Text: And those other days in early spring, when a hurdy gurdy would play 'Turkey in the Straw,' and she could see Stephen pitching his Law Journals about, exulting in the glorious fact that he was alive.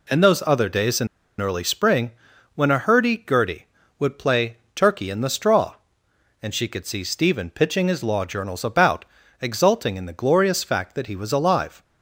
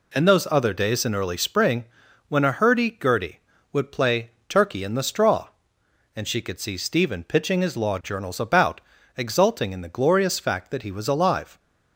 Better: second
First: pauses between "in" and "early"; slight; at 1.0 s; 0.33 s long // pauses between "play" and "Turkey"; slight; at 4.5 s; 0.18 s long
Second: pauses between "play" and "Turkey"; slight; at 4.3 s; 0.18 s long

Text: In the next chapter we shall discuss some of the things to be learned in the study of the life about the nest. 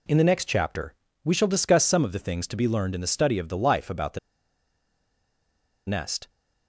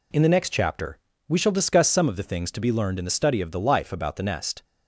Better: second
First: pauses between "chapter" and "we"; slight; at 0.9 s; 0.32 s long // pauses between "the" and "nest"; strong; at 4.1 s; 1.6 s long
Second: pauses between "chapter" and "we"; slight; at 0.9 s; 0.32 s long

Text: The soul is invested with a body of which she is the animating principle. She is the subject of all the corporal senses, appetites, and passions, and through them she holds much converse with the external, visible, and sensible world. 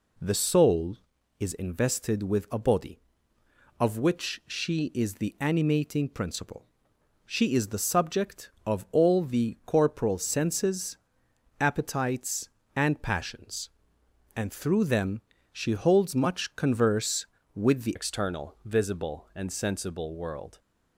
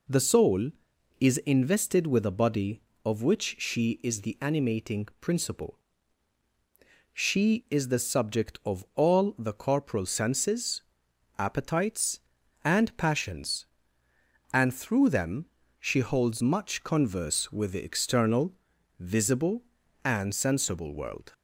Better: second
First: pauses between "them" and "she"; slight; at 15.2 s; 0.30 s long // changes voice at "external"; from 17.9 s on; 2.6 s long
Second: pauses between "them" and "she"; slight; at 15.4 s; 0.34 s long

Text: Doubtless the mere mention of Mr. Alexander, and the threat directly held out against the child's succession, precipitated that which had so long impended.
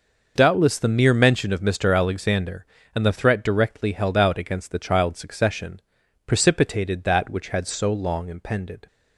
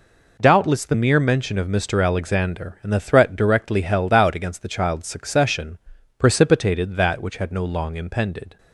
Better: first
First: none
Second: says "no" for "so"; at 7.5 s

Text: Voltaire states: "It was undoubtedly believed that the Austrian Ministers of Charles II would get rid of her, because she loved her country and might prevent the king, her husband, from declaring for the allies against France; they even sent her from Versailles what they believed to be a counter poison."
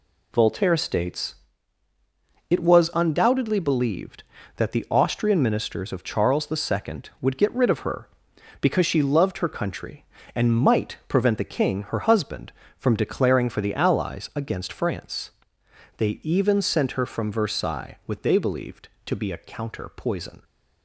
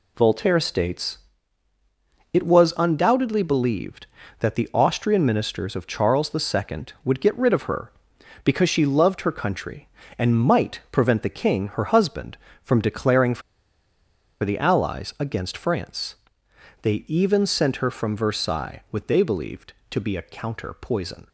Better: first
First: none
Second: pauses between "for" and "the"; at 13.4 s; 1.0 s long

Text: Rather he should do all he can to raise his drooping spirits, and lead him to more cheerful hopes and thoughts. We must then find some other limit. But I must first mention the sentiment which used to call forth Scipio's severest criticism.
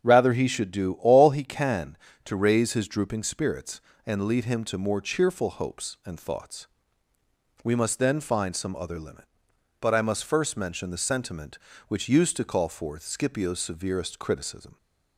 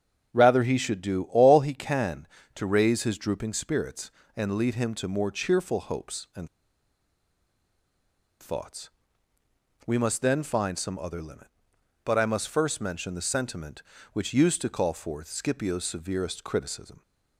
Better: first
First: starts louder than the rest; strong; until 1.1 s; 8 dB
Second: starts louder than the rest; strong; until 1.4 s; 8 dB // pauses between "and" and "thoughts"; strong; at 6.4 s; 1.9 s long

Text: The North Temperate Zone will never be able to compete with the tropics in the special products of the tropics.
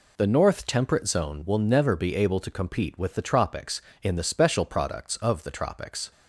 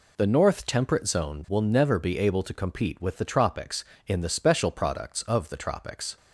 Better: neither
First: none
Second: none

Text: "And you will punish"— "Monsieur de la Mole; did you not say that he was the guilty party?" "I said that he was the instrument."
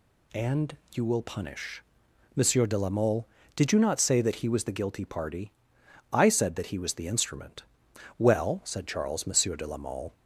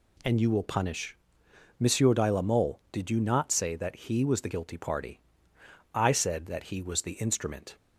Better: second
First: pauses between "And" and "you"; slight; at 0.7 s; 0.16 s long // goes on to say "Well said Charles Monsieur de la Mole"; strong; from 8.1 s on; 1.9 s long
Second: none

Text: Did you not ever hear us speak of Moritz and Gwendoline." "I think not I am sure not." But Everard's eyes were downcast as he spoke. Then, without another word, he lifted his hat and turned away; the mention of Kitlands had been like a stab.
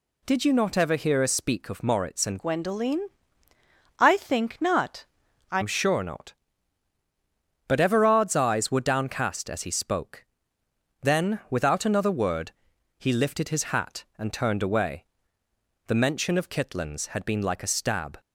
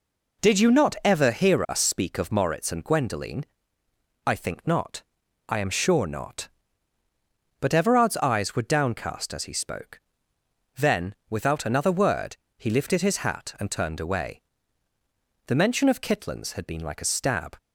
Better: second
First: changes voice from "Gwendoline" to "I"; from 2.3 to 5.6 s; 3.3 s long // pauses between "not" and "I"; at 5.0 s; 0.44 s long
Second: pauses between "not" and "I"; at 5.0 s; 0.44 s long

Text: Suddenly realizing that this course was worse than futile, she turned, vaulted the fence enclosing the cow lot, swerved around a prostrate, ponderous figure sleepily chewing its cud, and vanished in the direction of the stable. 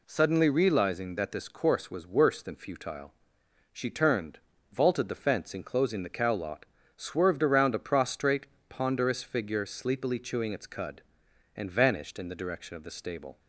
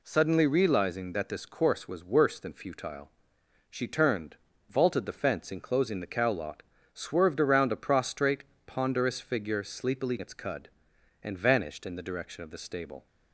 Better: first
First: none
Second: skips "chewing"; at 10.1 s

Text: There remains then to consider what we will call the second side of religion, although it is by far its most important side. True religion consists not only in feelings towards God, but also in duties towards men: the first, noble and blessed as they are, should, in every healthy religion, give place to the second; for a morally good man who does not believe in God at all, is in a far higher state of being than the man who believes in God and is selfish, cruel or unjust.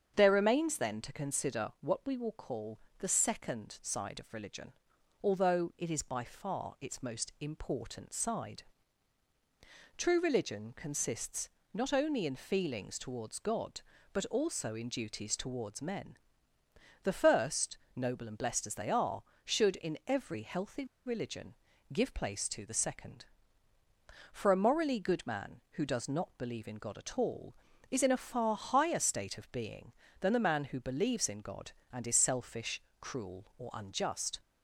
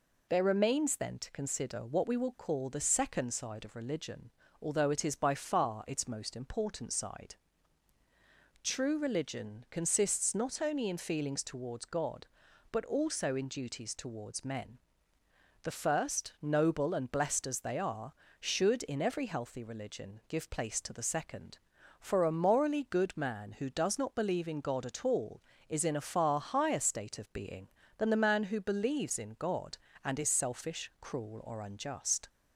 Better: second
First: starts louder than the rest; strong; until 1.1 s; 7.5 dB // pauses between "call" and "the"; slight; at 2.7 s; 0.20 s long // pauses between "consists" and "not"; slight; at 11.4 s; 0.24 s long // pauses between "healthy" and "religion"; slight; at 20.8 s; 0.21 s long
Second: none

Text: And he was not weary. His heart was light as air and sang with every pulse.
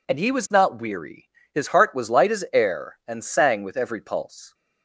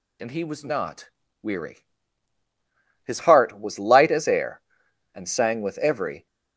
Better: first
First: none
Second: pauses between "not" and "weary"; slight; at 1.0 s; 0.32 s long // stops before "pulse"; at 6.2 s

